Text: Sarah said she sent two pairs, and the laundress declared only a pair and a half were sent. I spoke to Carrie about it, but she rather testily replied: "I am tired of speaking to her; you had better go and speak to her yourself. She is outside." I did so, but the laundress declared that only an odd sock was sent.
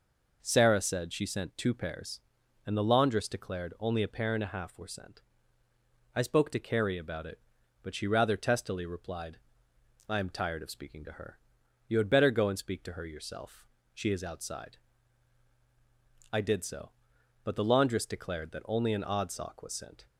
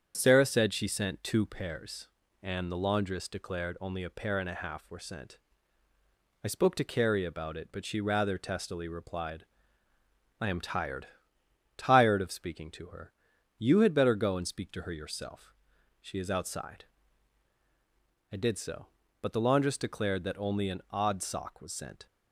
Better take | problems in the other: first | starts louder than the rest; strong; until 1.1 s; 8 dB // says "tired" twice; at 11.7 s

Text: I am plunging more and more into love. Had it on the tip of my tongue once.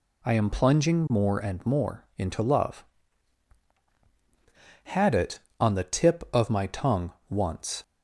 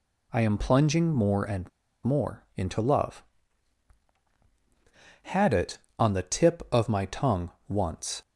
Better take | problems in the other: first | pauses between "and" and "more"; slight; at 1.6 s; 0.35 s long // pauses between "tongue" and "once"; slight; at 7.5 s; 0.16 s long; slight in the first

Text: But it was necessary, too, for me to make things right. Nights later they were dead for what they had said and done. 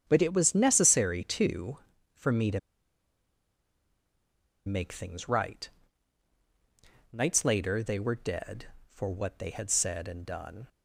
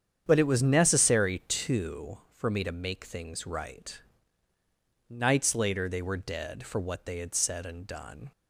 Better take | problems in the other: second | starts louder than the rest; strong; until 1.0 s; 8.5 dB; strong in the second // pauses between "to" and "make"; strong; at 2.5 s; 2.0 s long

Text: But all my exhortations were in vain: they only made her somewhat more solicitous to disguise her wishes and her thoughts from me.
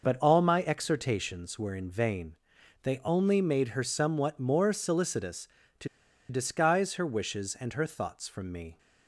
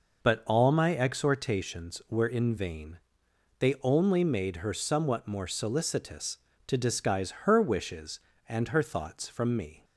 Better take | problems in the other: second | pauses between "to" and "disguise"; at 5.8 s; 0.42 s long

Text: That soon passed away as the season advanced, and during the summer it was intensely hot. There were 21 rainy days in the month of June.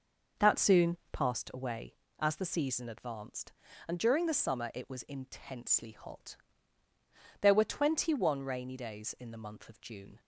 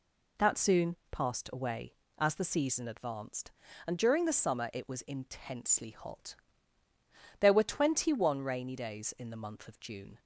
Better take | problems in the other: second | starts louder than the rest; noticeable; until 1.6 s; 6 dB

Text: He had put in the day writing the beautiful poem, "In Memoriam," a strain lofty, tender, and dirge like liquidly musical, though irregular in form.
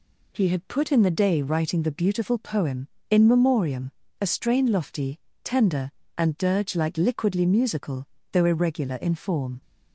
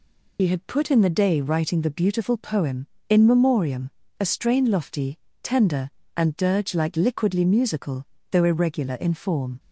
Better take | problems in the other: first | loses the start of "He"; at 0.3 s; 65 ms

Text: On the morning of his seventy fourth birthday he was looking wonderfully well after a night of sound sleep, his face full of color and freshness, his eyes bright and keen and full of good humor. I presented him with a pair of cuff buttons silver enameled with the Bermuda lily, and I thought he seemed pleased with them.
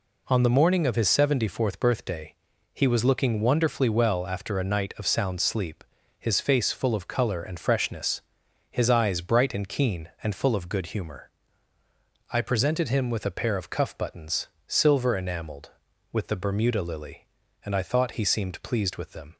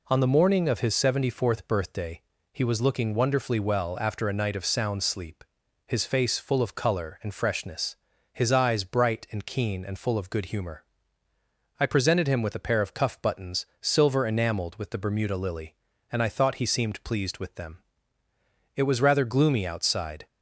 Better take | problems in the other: first | pauses between "birthday" and "he"; slight; at 2.2 s; 0.32 s long; also in the first // pauses between "buttons" and "silver"; slight; at 13.6 s; 0.16 s long; slight in the first // goes on to say "It was rather gloomy outside"; from 18.7 s on; 1.5 s long

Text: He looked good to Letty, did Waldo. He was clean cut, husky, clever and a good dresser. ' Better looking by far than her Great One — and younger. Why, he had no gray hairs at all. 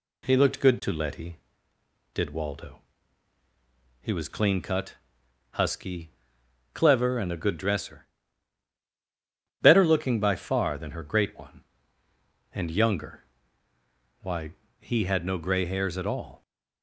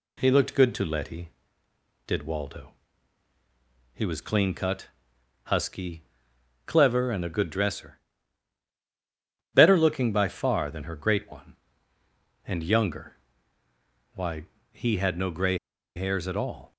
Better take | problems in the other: first | pauses between "gray" and "hairs"; at 15.5 s; 0.37 s long

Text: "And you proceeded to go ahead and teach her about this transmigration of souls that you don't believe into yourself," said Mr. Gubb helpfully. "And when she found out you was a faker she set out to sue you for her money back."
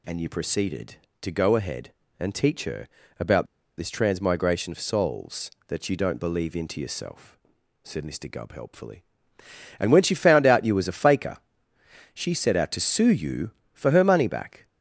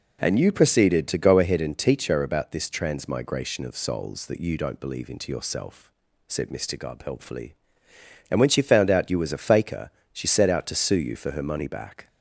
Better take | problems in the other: second | pauses between "her" and "about"; slight; at 2.8 s; 0.32 s long // pauses between "about" and "this"; slight; at 3.4 s; 0.32 s long // pauses between "faker" and "she"; noticeable; at 11.3 s; 0.74 s long; slight in the second

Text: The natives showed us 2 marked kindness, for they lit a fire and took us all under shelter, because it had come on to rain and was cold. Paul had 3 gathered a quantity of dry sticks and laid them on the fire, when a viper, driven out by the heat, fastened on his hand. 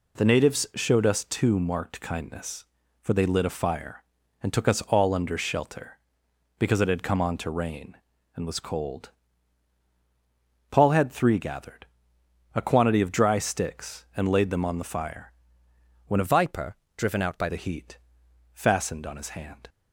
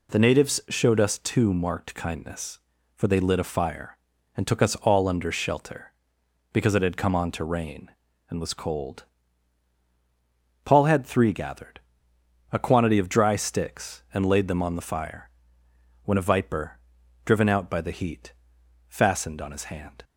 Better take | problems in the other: second | pauses between "gathered" and "a"; noticeable; at 11.8 s; 0.70 s long; noticeable in the second // changes voice from "viper" to "by"; from 16.2 to 17.4 s; 1.2 s long

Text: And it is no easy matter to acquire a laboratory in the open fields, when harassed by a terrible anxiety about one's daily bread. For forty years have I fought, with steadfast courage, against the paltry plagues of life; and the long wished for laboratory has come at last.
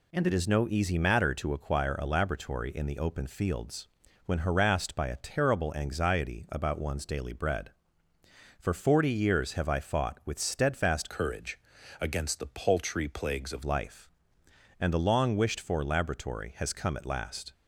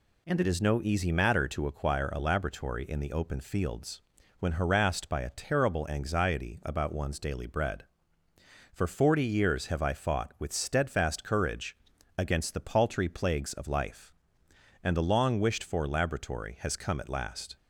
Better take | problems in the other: second | changes voice from "courage" to "of"; from 11.0 to 13.6 s; 2.6 s long

